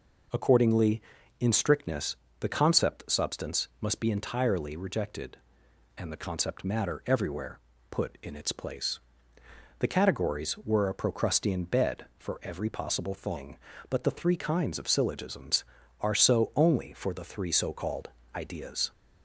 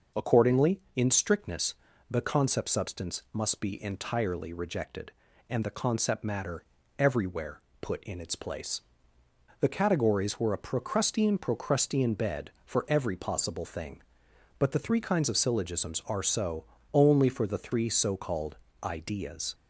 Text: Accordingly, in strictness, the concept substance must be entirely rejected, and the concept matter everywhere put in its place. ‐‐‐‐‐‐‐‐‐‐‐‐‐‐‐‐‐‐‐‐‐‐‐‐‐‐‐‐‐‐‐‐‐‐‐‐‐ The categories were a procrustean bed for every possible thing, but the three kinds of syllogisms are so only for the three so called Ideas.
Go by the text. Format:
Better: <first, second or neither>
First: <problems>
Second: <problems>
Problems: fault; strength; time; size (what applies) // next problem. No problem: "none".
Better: first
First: pauses between "everywhere" and "put"; slight; at 7.5 s; 0.30 s long // pauses between "called" and "Ideas"; slight; at 18.0 s; 0.26 s long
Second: starts louder than the rest; until 1.3 s; 6 dB // pauses between "matter" and "everywhere"; slight; at 6.6 s; 0.34 s long // pauses between "everywhere" and "put"; slight; at 7.6 s; 0.20 s long // says "procrustean" twice; at 11.3 s // pauses between "so" and "only"; slight; at 16.6 s; 0.28 s long // pauses between "called" and "Ideas"; slight; at 18.5 s; 0.26 s long